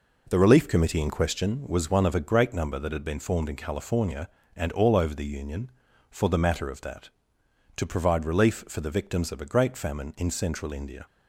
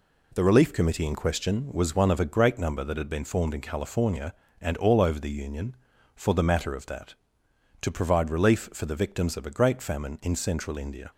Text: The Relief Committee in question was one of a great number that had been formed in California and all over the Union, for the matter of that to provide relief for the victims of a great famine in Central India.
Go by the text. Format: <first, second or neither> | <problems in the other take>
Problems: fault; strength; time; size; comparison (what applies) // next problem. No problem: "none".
second | starts louder than the rest; noticeable; until 1.4 s; 4.5 dB